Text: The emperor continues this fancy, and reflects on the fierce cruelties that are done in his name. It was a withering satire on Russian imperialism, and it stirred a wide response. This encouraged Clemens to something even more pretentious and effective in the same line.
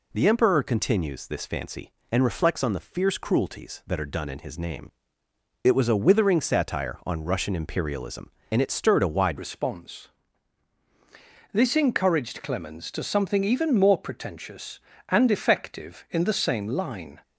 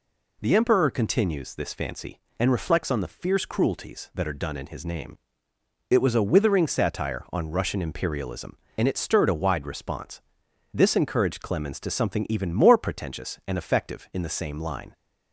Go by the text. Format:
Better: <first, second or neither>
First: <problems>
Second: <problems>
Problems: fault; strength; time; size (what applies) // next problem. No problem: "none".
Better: second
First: changes voice at "response"; from 9.3 s on; 7.9 s long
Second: none